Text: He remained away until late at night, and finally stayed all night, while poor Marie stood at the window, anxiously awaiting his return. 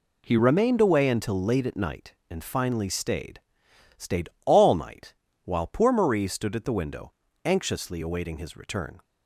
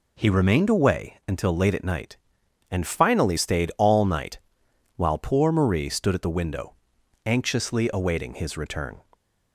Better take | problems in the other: second | says "stayed" twice; at 3.9 s

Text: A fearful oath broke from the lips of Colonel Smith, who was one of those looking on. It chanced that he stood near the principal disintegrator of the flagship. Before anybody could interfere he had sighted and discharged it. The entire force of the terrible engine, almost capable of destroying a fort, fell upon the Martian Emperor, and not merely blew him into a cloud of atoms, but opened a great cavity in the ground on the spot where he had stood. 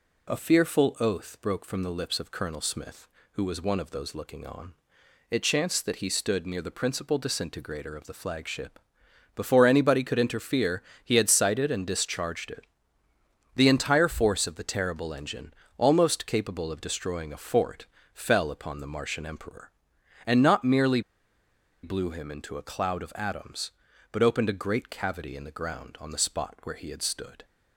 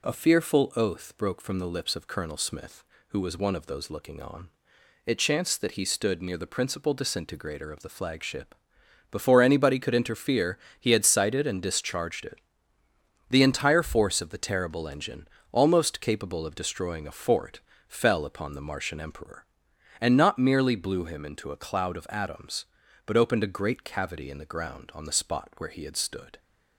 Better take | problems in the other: second | pauses between "interfere" and "he"; slight; at 10.8 s; 0.20 s long; slight in the second // pauses between "merely" and "blew"; noticeable; at 21.0 s; 0.82 s long

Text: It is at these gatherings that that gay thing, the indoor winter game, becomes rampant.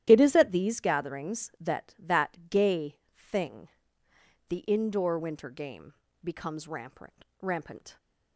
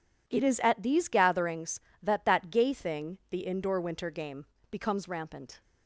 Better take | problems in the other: second | starts louder than the rest; strong; until 1.0 s; 12 dB // pauses between "gay" and "thing"; slight; at 2.9 s; 0.18 s long // says "rampant" twice; at 7.4 s

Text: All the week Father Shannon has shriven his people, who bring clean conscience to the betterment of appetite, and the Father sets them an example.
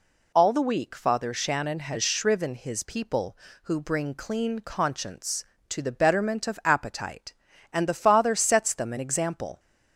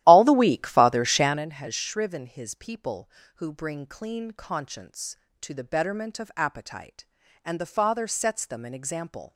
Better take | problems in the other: first | starts louder than the rest; strong; until 1.5 s; 14 dB

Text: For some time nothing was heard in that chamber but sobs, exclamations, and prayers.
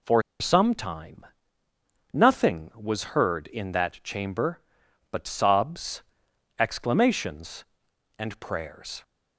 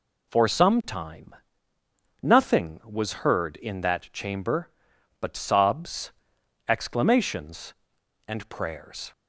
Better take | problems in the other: second | pauses between "For" and "some"; slight; at 0.2 s; 0.19 s long // pauses between "time" and "nothing"; noticeable; at 1.2 s; 0.88 s long; noticeable in the second

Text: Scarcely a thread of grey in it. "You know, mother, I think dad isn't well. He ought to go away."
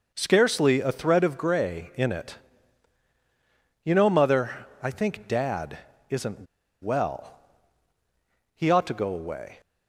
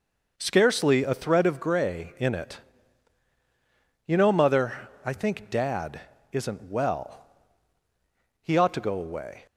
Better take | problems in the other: second | pauses between "dad" and "isn't"; slight; at 5.7 s; 0.32 s long; slight in the second // pauses between "isn't" and "well"; at 6.4 s; 0.37 s long

